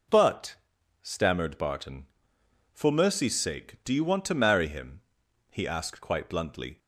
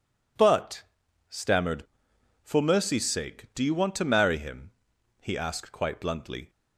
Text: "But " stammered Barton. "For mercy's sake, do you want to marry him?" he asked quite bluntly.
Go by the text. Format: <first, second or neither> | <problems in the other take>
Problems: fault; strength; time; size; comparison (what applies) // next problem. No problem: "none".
first | skips "Barton"; at 2.1 s